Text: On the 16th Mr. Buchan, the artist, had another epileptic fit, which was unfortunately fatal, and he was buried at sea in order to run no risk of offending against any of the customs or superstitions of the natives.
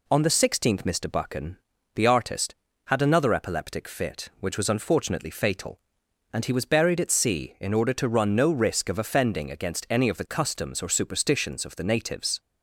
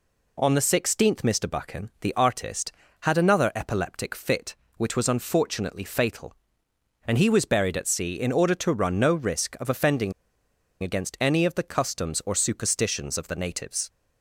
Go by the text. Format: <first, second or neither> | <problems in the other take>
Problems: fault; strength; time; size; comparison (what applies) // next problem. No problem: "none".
first | pauses between "offending" and "against"; noticeable; at 10.1 s; 0.69 s long